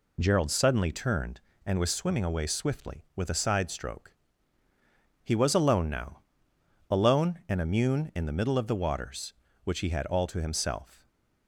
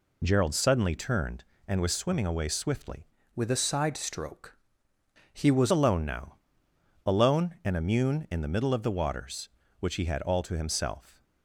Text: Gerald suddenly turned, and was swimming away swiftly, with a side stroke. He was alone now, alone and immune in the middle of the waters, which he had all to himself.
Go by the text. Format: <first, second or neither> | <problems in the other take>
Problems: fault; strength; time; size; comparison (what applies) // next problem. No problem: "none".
first | changes voice from "with" to "was"; from 3.3 to 5.7 s; 2.4 s long